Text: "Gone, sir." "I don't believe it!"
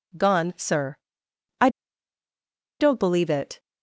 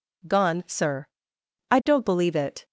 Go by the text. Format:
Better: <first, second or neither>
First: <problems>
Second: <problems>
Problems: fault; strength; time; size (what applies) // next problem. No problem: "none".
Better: second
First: pauses between "I" and "don't"; at 1.6 s; 1.1 s long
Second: none